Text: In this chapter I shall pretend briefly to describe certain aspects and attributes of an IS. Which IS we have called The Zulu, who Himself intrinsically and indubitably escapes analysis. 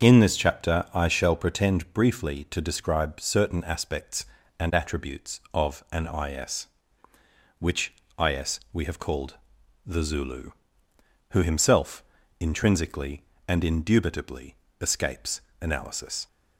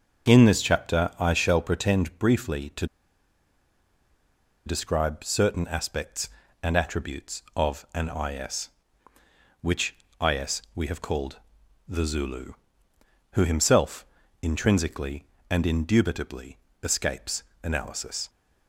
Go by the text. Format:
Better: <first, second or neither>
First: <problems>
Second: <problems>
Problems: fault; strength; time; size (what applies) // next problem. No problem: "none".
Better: first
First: starts louder than the rest; until 1.1 s; 7 dB // pauses between "called" and "The"; noticeable; at 9.3 s; 0.50 s long // pauses between "Himself" and "intrinsically"; at 12.0 s; 0.38 s long // pauses between "indubitably" and "escapes"; slight; at 14.5 s; 0.24 s long // pauses between "escapes" and "analysis"; slight; at 15.3 s; 0.22 s long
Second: starts louder than the rest; until 1.3 s; 7 dB // pauses between "to" and "describe"; strong; at 2.8 s; 1.8 s long // pauses between "called" and "The"; noticeable; at 11.3 s; 0.50 s long // pauses between "Himself" and "intrinsically"; at 14.0 s; 0.38 s long // pauses between "indubitably" and "escapes"; slight; at 16.5 s; 0.24 s long // pauses between "escapes" and "analysis"; slight; at 17.4 s; 0.22 s long